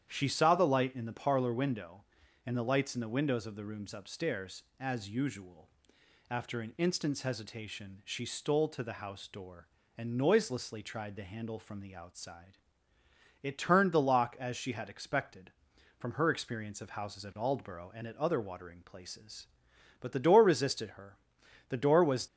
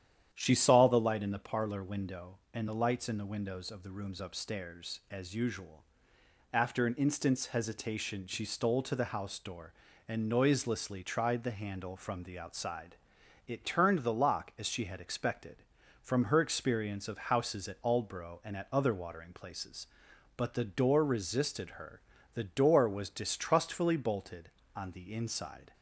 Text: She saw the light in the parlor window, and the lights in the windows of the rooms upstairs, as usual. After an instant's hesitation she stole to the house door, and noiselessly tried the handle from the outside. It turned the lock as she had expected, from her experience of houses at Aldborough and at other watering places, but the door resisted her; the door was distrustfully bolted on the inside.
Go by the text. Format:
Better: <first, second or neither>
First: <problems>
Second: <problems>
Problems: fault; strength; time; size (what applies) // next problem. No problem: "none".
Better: second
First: starts louder than the rest; strong; until 1.1 s; 9.5 dB // stops before "distrustfully bolted on the inside"; at 22.2 s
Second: starts louder than the rest; strong; until 1.3 s; 10 dB